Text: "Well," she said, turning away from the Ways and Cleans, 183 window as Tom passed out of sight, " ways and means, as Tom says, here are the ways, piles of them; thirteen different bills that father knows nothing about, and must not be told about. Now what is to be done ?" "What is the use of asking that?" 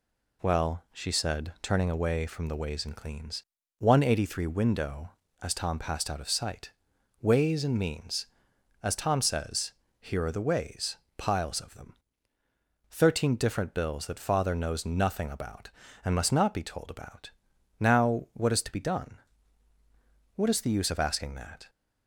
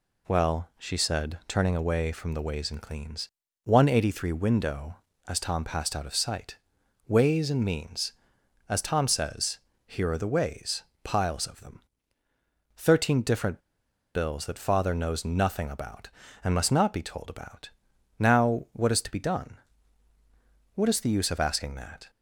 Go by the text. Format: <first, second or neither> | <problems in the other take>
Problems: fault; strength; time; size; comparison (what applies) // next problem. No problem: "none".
first | pauses between "different" and "bills"; noticeable; at 13.5 s; 0.55 s long